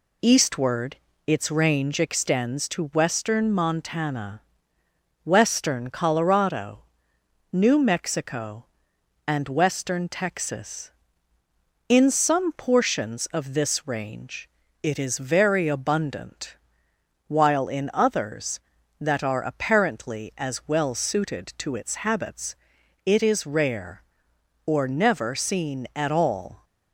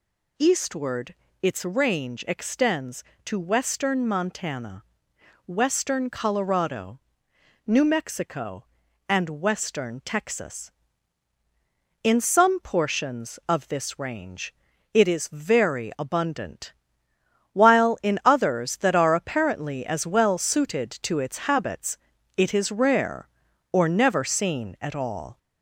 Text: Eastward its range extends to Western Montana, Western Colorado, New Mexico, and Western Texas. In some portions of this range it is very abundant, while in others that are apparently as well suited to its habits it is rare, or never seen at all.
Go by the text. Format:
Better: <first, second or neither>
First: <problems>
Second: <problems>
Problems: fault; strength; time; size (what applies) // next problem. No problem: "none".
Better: first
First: pauses between "Eastward" and "its"; slight; at 0.9 s; 0.32 s long // pauses between "range" and "it"; slight; at 14.4 s; 0.32 s long // pauses between "habits" and "it"; noticeable; at 22.5 s; 0.50 s long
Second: gets louder; slight; throughout; 3 dB // pauses between "Eastward" and "its"; slight; at 1.1 s; 0.28 s long // pauses between "range" and "it"; at 14.5 s; 0.38 s long // pauses between "habits" and "it"; at 21.9 s; 0.40 s long